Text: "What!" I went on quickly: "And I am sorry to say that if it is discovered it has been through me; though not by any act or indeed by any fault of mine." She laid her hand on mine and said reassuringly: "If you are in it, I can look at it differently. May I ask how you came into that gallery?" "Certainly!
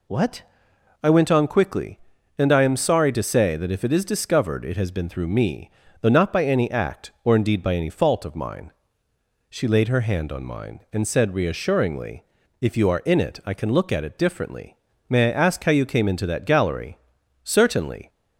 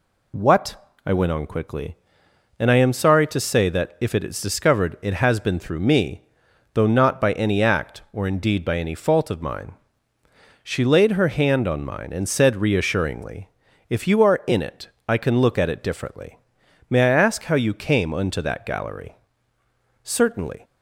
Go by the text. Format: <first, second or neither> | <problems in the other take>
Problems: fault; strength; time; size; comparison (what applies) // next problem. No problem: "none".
first | says "unto" for "into"; at 18.1 s